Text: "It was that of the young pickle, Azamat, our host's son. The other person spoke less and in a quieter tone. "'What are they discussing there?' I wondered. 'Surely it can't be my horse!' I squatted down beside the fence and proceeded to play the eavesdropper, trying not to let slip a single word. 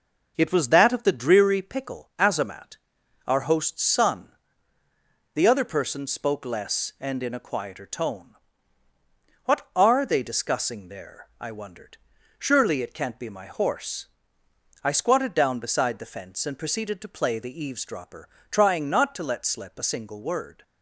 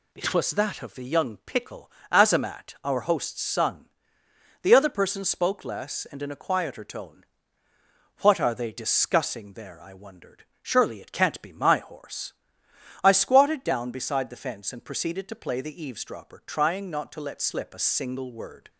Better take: second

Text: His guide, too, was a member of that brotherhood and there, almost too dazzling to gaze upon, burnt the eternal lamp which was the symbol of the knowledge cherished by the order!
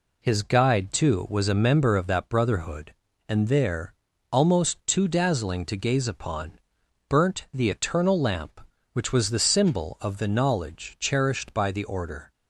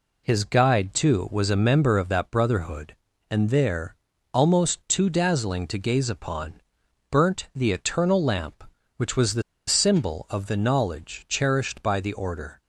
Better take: first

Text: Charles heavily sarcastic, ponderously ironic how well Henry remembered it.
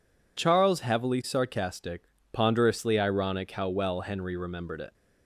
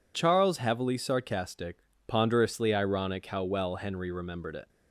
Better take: neither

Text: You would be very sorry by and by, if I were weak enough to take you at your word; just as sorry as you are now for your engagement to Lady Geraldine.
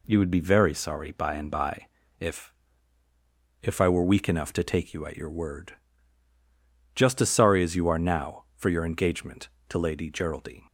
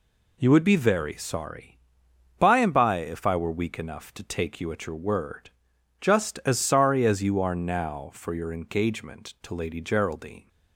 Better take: second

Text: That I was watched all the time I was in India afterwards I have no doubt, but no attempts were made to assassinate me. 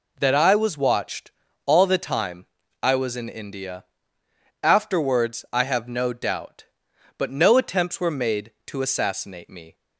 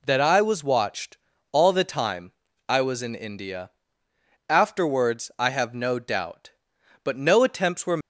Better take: first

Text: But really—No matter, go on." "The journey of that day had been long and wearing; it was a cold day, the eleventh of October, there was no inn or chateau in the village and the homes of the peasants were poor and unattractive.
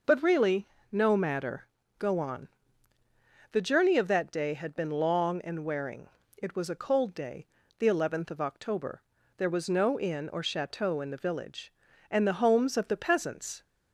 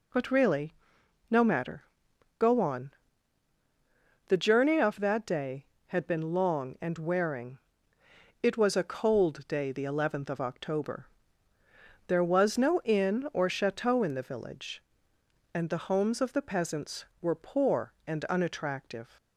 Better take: second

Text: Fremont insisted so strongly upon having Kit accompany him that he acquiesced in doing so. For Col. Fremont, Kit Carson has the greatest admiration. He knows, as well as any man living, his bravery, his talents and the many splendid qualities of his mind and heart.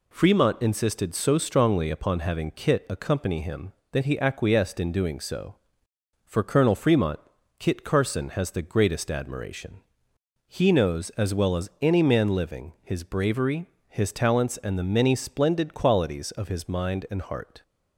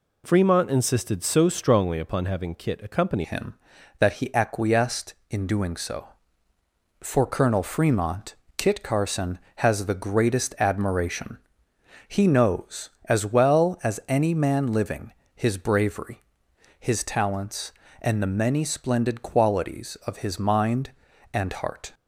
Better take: first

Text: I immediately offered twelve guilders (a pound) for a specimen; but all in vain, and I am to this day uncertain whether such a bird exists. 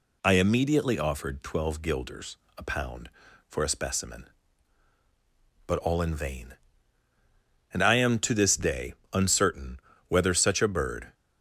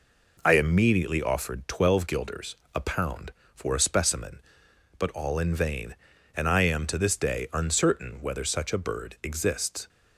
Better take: second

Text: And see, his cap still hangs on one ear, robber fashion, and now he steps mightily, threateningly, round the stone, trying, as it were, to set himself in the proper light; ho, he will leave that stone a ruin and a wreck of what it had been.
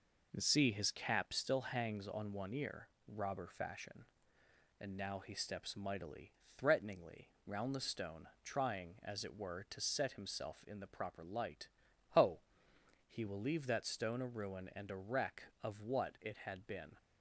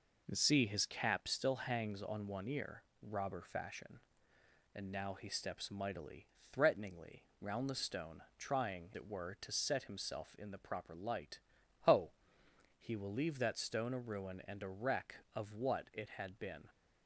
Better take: first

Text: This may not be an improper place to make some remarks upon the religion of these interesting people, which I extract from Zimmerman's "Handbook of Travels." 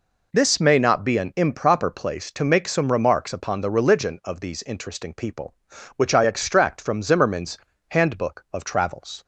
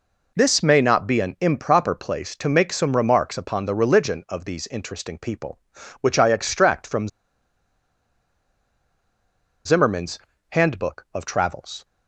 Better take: first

